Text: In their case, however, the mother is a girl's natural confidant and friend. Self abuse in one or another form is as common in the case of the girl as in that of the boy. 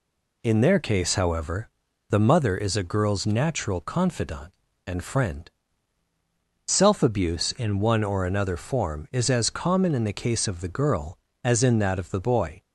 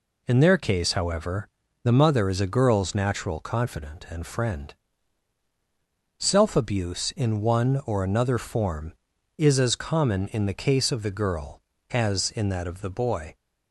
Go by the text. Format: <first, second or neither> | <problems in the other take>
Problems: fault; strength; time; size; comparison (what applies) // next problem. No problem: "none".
neither | none